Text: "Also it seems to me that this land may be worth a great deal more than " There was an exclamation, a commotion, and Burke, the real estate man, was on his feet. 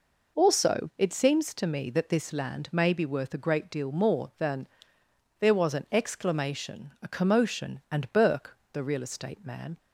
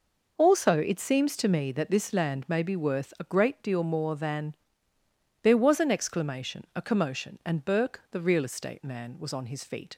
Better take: second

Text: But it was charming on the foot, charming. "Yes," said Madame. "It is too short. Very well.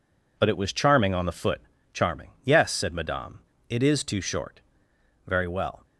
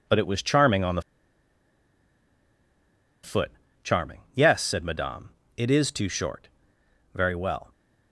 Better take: first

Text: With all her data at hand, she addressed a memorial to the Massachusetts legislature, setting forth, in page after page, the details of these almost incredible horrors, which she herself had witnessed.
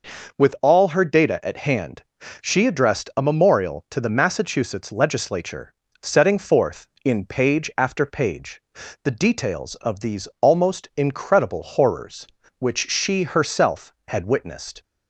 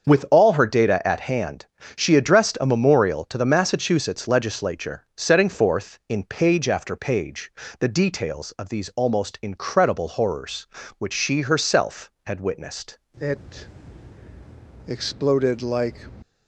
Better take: first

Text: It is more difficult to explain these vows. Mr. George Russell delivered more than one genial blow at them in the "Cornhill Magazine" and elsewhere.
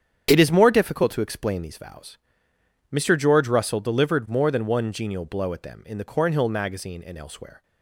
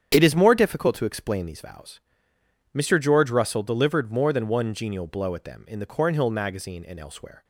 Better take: neither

